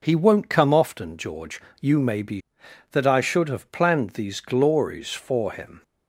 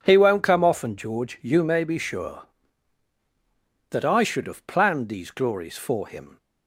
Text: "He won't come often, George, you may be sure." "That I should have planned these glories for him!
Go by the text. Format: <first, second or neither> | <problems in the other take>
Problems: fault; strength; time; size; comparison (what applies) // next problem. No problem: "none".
second | skips "sure"; at 2.6 s